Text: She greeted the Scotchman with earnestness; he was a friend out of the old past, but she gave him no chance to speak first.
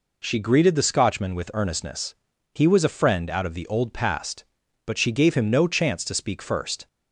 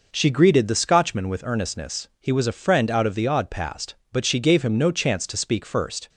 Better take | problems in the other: first | says "odd" for "old"; at 3.2 s

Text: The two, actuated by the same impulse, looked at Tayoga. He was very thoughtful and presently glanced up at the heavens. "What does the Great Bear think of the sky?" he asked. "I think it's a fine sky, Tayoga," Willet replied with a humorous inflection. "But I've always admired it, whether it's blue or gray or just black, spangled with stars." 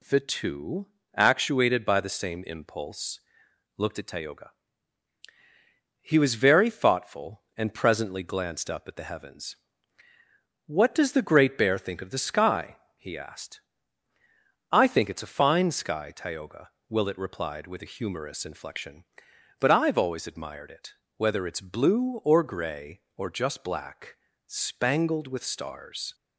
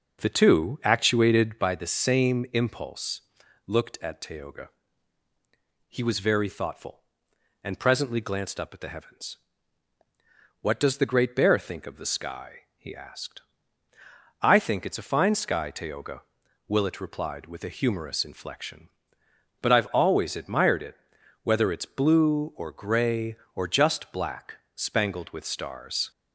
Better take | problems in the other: first | starts louder than the rest; noticeable; until 1.7 s; 5.5 dB

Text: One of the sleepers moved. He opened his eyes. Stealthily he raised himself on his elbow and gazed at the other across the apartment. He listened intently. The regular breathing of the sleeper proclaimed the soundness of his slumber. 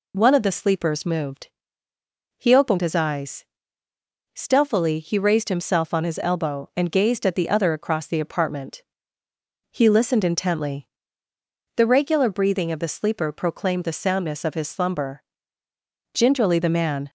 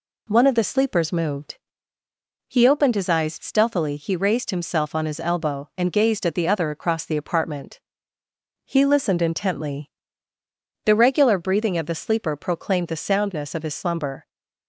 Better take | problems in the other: second | goes on to say "Gingerly the man"; noticeable; from 16.1 s on; 0.96 s long

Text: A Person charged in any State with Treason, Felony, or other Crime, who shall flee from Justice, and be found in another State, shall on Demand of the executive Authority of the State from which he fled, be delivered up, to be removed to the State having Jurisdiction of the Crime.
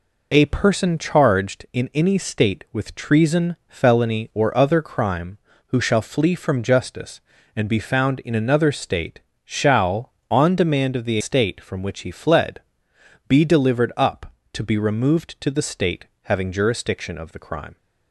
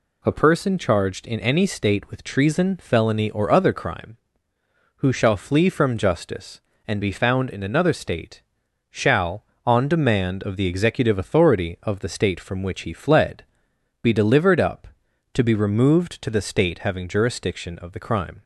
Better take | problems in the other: second | skips "executive Authority of the"; at 11.2 s // pauses between "State" and "having"; slight; at 16.0 s; 0.20 s long

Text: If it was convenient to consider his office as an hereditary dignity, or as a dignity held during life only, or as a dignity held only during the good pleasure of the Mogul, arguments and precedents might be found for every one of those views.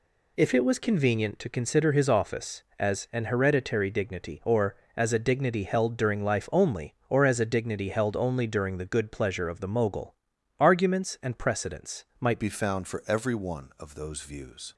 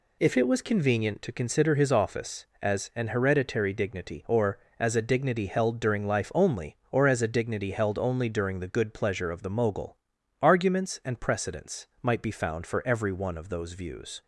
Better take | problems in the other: second | pauses between "precedents" and "might"; slight; at 12.0 s; 0.16 s long; slight in the second // changes voice at "be"; from 12.3 s on; 2.4 s long

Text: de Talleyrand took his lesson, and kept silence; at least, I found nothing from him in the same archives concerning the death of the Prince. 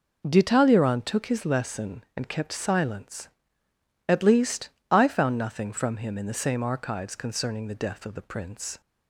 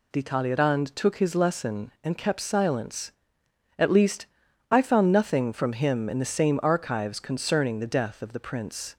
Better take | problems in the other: neither | none

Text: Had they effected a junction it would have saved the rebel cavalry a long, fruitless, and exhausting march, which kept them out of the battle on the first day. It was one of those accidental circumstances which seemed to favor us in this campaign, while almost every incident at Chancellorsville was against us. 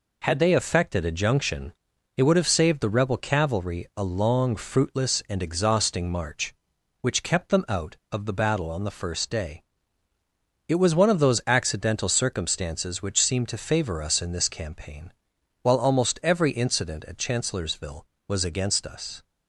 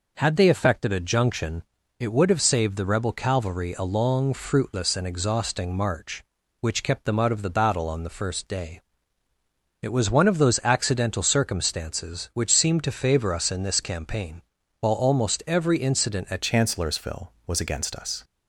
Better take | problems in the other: first | pauses between "junction" and "it"; slight; at 1.6 s; 0.34 s long; also in the first // changes voice at "Chancellorsville"; from 16.4 s on; 1.8 s long

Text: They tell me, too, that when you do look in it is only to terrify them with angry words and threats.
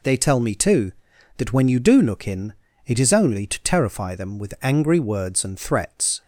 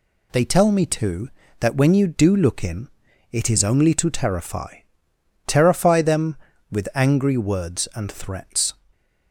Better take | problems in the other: first | pauses between "in" and "it"; at 2.8 s; 0.44 s long; slight in the first // says "terrify" twice; at 5.4 s // stays silent after the last word; slight; from 8.7 s on; 0.6 s long

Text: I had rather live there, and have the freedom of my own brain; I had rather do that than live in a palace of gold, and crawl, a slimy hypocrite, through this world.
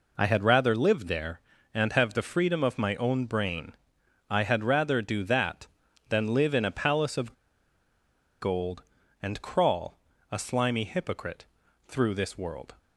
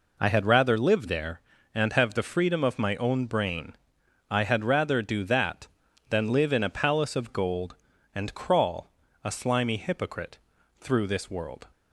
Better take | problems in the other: second | pauses between "of" and "gold"; at 7.3 s; 1.0 s long

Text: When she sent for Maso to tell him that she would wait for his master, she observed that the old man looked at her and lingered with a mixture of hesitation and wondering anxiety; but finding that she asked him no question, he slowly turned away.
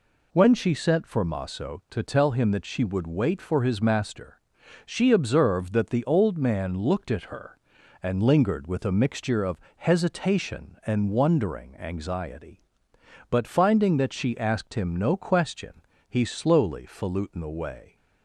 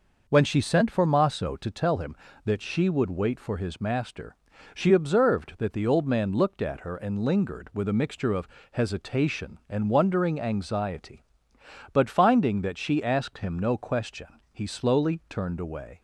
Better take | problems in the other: second | pauses between "of" and "hesitation"; slight; at 9.5 s; 0.20 s long; slight in the second // says "falutin" for "turned"; at 16.8 s

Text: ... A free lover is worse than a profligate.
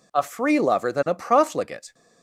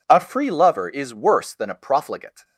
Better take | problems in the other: second | skips "is worse"; at 0.9 s

